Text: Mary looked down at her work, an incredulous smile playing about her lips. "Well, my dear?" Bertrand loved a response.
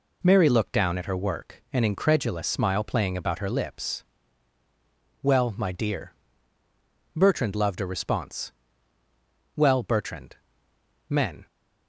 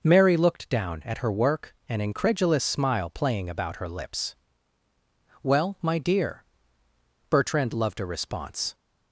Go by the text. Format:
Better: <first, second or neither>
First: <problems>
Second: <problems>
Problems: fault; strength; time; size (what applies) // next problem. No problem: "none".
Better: second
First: goes on to say "Well Bertrand Men"; strong; from 9.5 s on; 1.9 s long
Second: none